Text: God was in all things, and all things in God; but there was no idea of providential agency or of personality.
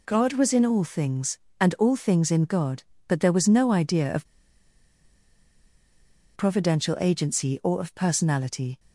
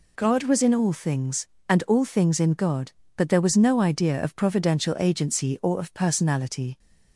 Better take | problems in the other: second | pauses between "of" and "providential"; strong; at 4.2 s; 2.0 s long

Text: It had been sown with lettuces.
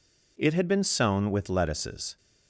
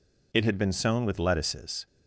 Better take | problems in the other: neither | none

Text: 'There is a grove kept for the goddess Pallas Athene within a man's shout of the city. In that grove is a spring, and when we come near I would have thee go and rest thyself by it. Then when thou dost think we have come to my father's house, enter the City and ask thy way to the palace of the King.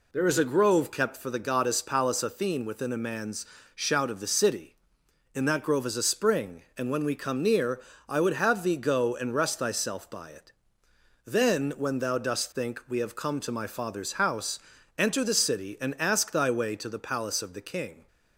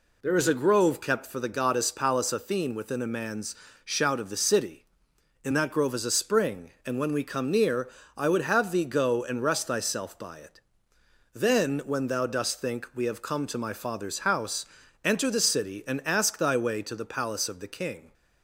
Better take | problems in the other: neither | pauses between "man's" and "shout"; slight; the same in both // pauses between "near" and "I"; slight; the same in both

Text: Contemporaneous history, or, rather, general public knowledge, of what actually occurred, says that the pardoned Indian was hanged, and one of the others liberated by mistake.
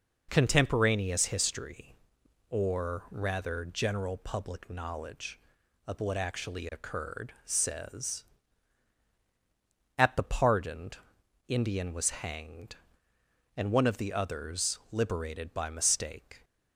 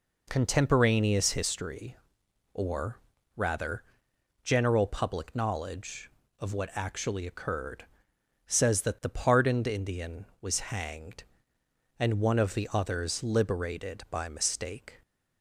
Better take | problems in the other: second | says "at" for "that"; at 9.9 s // pauses between "pardoned" and "Indian"; noticeable; at 10.9 s; 0.52 s long

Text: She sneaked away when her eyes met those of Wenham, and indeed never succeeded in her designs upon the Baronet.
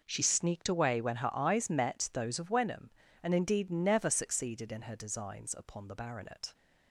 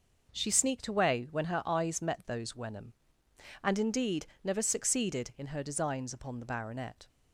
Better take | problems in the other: first | skips "of"; at 2.5 s // pauses between "indeed" and "never"; slight; at 4.2 s; 0.18 s long

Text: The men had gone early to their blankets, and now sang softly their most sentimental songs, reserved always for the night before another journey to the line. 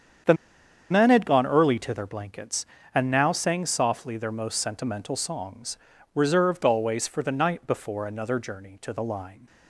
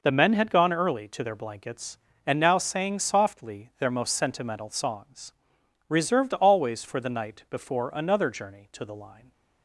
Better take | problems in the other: second | starts louder than the rest; strong; until 1.8 s; 8 dB // pauses between "The" and "men"; noticeable; at 0.3 s; 0.56 s long

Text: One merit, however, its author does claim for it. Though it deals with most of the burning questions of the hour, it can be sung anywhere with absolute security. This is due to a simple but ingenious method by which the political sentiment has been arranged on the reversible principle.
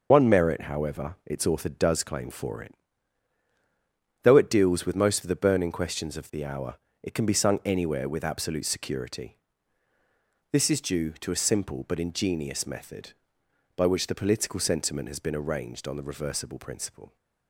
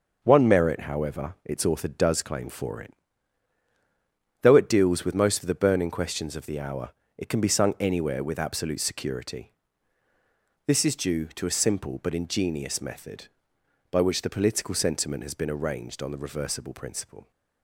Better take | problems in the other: second | loses the start of "One"; at 0.1 s; 50 ms // starts louder than the rest; noticeable; until 1.1 s; 6 dB; noticeable in the second

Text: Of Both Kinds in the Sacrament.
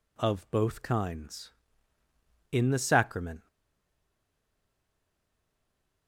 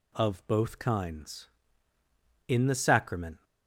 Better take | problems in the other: second | stays silent after the last word; strong; from 3.4 s on; 2.6 s long

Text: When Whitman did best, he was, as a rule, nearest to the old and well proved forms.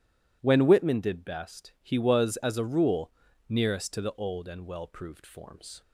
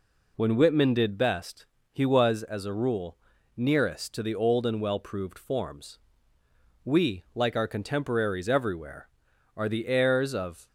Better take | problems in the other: first | goes on to say "We like our contemporaries everywhere are the heirs of"; strong; from 6.8 s on; 3.8 s long

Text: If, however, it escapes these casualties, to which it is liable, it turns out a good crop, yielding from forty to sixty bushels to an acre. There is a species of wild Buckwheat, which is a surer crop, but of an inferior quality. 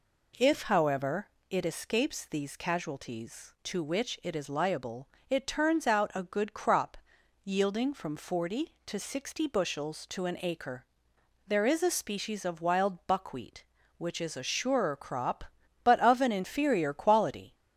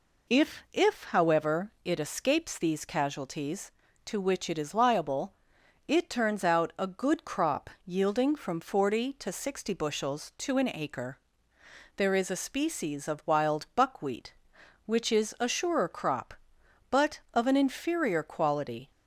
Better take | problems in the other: first | says "If" twice; at 0.7 s

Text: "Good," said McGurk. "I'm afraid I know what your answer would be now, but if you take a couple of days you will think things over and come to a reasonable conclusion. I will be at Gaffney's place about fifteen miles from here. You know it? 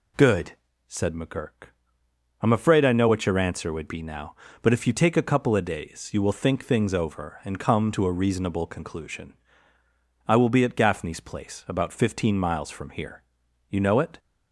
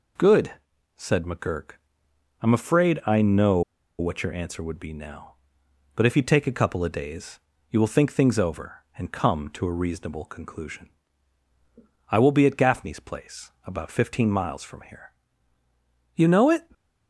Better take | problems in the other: first | pauses between "know" and "what"; at 3.6 s; 0.38 s long // pauses between "days" and "you"; slight; at 7.3 s; 0.30 s long // pauses between "place" and "about"; slight; at 13.4 s; 0.16 s long

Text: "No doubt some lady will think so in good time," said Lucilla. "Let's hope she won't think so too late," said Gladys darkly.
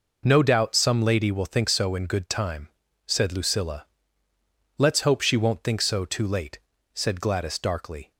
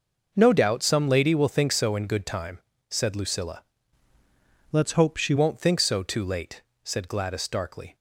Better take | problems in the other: first | changes voice from "Let's" to "she"; from 4.7 to 5.3 s; 0.6 s long

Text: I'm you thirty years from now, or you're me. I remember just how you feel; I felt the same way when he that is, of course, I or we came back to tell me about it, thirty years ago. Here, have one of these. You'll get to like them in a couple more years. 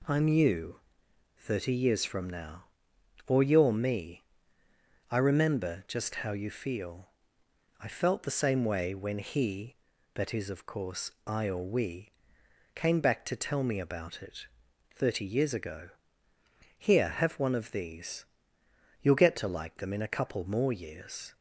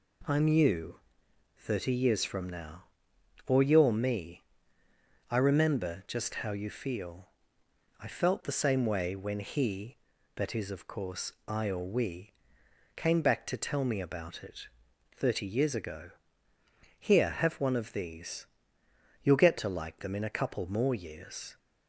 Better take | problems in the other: neither | pauses between "you" and "thirty"; noticeable; the same in both // pauses between "we" and "came"; noticeable; the same in both

